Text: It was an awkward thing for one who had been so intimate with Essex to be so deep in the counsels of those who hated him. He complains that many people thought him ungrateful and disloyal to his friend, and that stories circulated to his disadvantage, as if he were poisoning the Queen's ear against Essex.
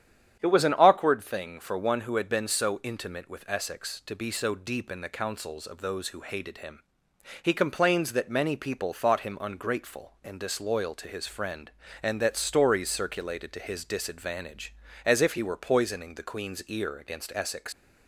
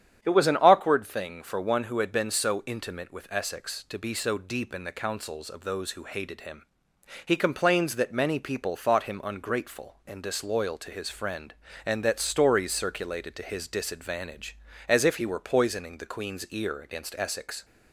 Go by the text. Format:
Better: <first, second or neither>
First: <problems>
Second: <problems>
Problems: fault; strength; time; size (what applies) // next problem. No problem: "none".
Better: second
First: starts louder than the rest; strong; until 1.4 s; 9 dB // leaves "Essex" unfinished; at 17.7 s; 90 ms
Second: starts louder than the rest; strong; until 1.2 s; 9 dB